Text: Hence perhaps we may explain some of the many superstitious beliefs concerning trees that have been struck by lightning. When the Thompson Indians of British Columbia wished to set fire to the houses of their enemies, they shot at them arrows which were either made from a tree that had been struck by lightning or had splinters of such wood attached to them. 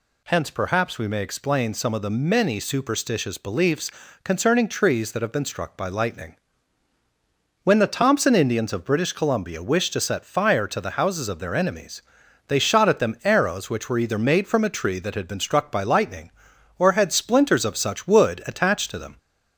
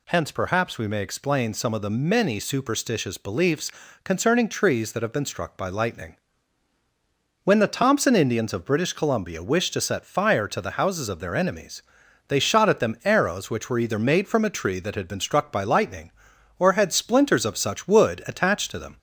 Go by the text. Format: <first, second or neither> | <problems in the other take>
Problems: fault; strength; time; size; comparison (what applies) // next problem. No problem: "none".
neither | pauses between "beliefs" and "concerning"; slight; the same in both